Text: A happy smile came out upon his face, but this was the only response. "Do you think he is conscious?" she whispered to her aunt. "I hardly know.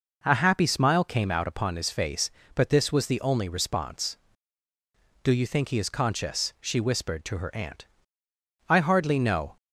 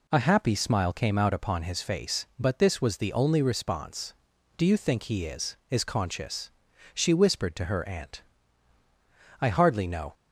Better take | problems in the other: first | says "is" twice; at 5.6 s

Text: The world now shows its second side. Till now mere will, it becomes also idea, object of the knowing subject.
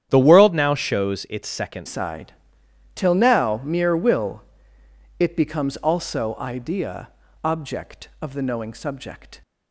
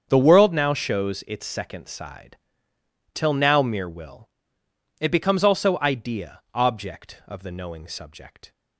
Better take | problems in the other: second | starts louder than the rest; strong; until 1.1 s; 10 dB; strong in the second // changes voice at "side"; from 1.8 s on; 7.6 s long

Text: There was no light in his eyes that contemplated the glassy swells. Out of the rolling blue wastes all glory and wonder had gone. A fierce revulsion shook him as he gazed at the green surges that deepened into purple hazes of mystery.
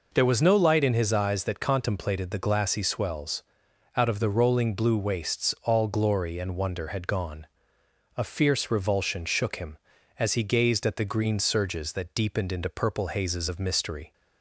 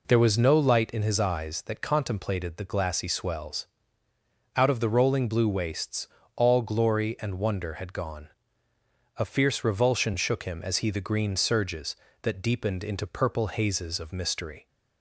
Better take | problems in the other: first | pauses between "wastes" and "all"; slight; at 6.0 s; 0.30 s long // skips "gazed at"; at 10.8 s

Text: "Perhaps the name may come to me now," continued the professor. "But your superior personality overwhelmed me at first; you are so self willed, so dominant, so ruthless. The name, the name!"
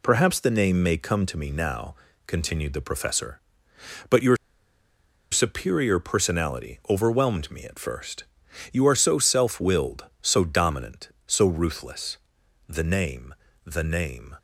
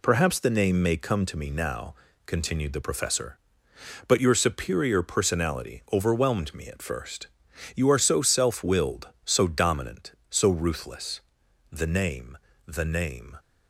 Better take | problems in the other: second | pauses between "your" and "superior"; noticeable; at 4.3 s; 0.95 s long

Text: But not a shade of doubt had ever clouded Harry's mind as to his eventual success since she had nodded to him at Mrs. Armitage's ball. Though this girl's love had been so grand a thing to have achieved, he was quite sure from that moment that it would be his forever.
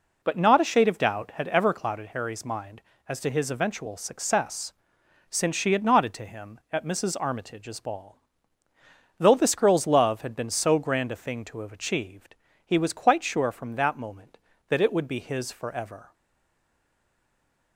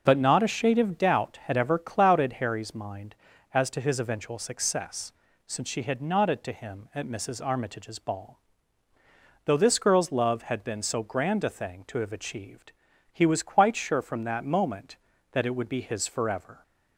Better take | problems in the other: second | pauses between "success" and "since"; noticeable; at 4.7 s; 0.56 s long; also in the second // stays silent after the last word; noticeable; from 16.1 s on; 1.6 s long

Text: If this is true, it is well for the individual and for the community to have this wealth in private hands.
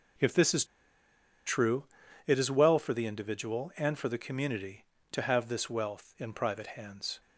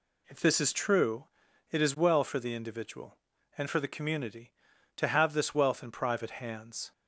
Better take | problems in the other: second | pauses between "is" and "true"; noticeable; at 0.6 s; 0.81 s long

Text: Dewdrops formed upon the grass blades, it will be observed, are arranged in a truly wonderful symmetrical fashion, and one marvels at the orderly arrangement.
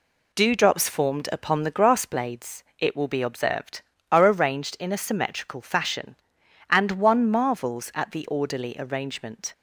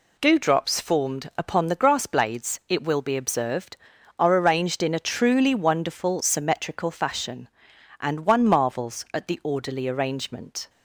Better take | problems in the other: second | skips "truly wonderful"; at 4.9 s

